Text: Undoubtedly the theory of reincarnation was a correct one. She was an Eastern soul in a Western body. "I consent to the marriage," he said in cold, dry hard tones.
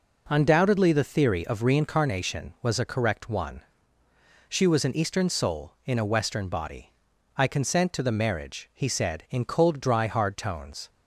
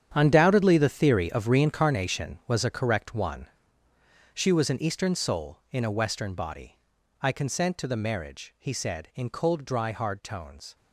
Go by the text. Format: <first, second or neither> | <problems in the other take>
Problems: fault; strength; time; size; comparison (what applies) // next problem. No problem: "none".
first | gets quieter; strong; throughout; 13.5 dB